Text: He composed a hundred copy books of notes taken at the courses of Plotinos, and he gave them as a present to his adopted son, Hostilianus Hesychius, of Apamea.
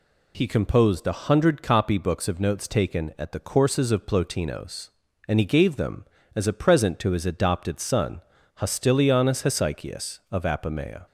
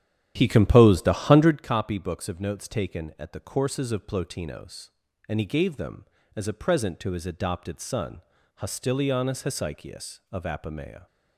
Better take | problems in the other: first | starts louder than the rest; strong; until 1.7 s; 11 dB

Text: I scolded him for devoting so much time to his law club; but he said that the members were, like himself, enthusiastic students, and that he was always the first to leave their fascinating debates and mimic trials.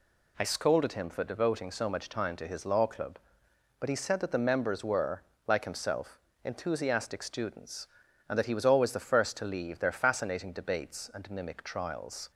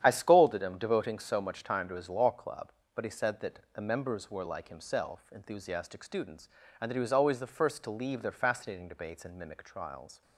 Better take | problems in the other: first | starts louder than the rest; strong; until 1.0 s; 9.5 dB // skips "for"; at 0.7 s // pauses between "that" and "the"; slight; at 3.5 s; 0.16 s long

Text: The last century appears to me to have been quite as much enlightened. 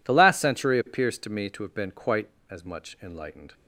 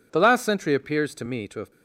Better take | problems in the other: first | stops before "been quite as much enlightened"; at 1.7 s

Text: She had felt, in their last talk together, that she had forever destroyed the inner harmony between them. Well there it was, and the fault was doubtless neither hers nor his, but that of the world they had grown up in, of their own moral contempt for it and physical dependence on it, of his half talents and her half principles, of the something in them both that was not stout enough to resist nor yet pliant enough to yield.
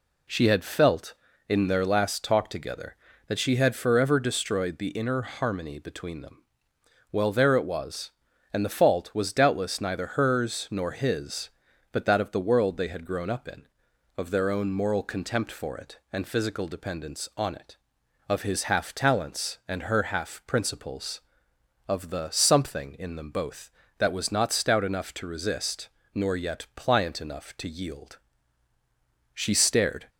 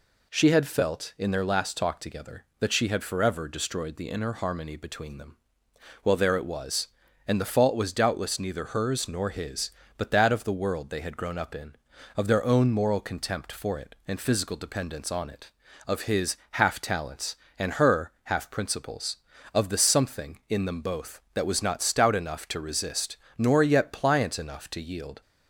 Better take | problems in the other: second | pauses between "resist" and "nor"; slight; at 25.8 s; 0.24 s long; slight in the second // goes on to say "She stared"; noticeable; from 29.3 s on; 0.76 s long

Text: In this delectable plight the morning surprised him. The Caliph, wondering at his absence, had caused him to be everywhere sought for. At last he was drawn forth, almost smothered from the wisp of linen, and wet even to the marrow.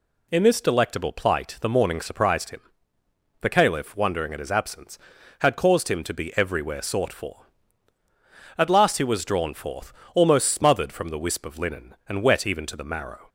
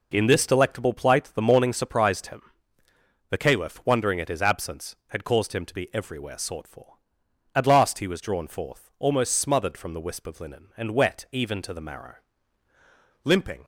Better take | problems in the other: first | goes on to say "Limping"; slight; from 13.2 s on; 0.40 s long

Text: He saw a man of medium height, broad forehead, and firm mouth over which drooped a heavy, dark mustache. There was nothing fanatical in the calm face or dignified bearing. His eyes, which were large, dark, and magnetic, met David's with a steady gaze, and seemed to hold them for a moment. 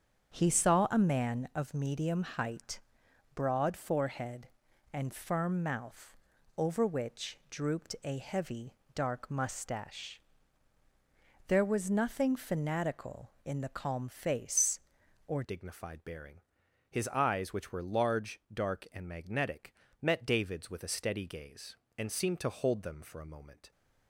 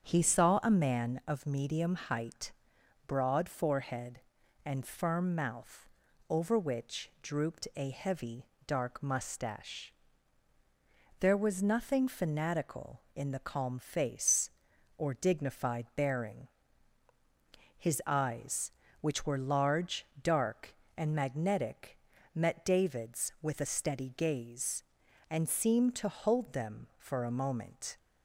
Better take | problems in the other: second | starts louder than the rest; strong; until 1.3 s; 8 dB; strong in the second // pauses between "mouth" and "over"; at 6.1 s; 0.40 s long; also in the second // changes voice at "dignified"; from 15.4 s on; 8.3 s long

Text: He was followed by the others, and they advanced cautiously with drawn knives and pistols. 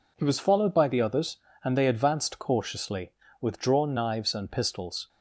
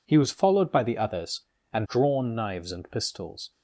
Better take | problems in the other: first | skips "they advanced cautiously with"; at 1.8 s

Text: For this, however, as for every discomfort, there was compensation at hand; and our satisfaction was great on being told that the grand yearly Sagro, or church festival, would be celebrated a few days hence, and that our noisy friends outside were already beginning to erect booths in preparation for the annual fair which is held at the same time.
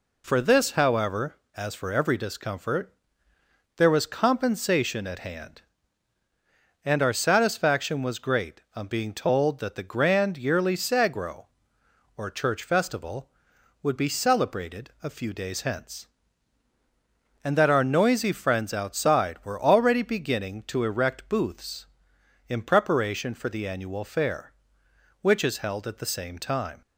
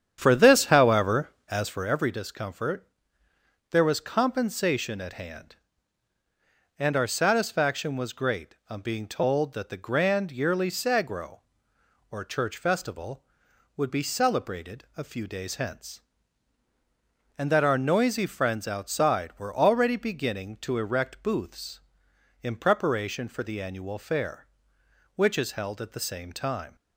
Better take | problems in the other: first | starts louder than the rest; strong; until 1.9 s; 9 dB

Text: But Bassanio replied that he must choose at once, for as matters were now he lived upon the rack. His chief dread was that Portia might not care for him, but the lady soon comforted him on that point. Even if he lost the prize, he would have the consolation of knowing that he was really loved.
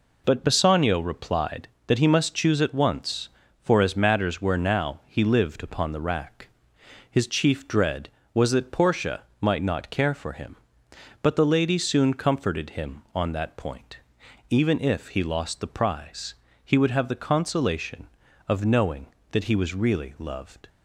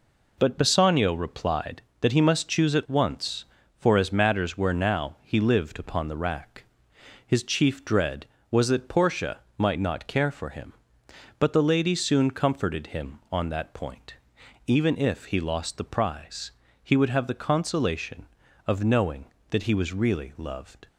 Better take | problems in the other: neither | pauses between "Portia" and "might"; slight; the same in both

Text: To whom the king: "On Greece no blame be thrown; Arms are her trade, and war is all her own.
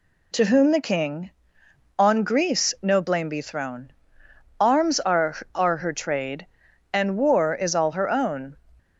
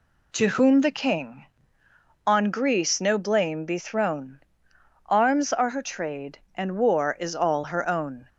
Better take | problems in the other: second | says "are" twice; at 5.5 s

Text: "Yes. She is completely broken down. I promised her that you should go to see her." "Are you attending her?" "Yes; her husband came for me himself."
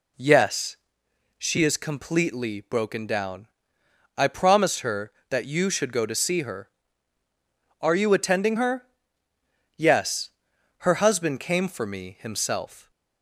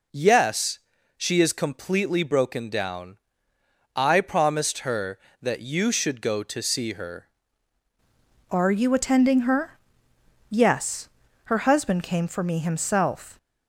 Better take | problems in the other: first | changes voice at "Are"; from 8.4 s on; 4.9 s long

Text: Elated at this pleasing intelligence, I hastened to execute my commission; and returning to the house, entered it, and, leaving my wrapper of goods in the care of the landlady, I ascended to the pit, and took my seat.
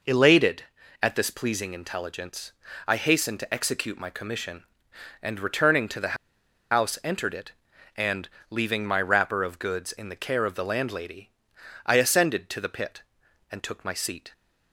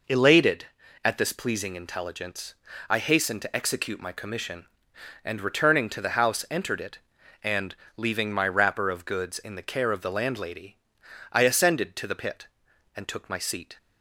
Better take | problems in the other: second | pauses between "the" and "house"; noticeable; at 6.1 s; 0.55 s long

